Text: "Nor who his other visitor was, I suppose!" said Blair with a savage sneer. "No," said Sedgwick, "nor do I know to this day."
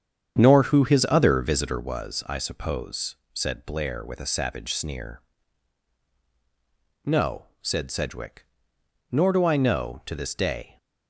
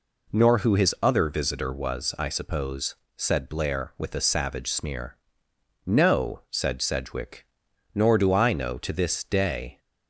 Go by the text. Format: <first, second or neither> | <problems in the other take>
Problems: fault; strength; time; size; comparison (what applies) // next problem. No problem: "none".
second | starts louder than the rest; strong; until 1.9 s; 8 dB